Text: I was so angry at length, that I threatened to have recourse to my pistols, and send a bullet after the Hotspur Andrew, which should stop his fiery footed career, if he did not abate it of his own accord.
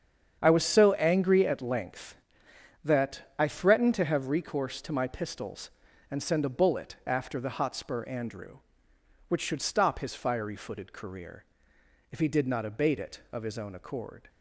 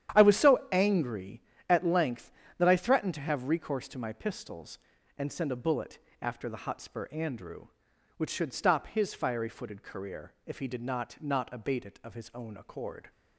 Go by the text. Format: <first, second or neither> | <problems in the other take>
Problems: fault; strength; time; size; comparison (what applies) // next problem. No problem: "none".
first | starts louder than the rest; strong; until 1.2 s; 10 dB; strong in the first // pauses between "bullet" and "after"; slight; at 5.9 s; 0.22 s long // says "not" twice; at 11.2 s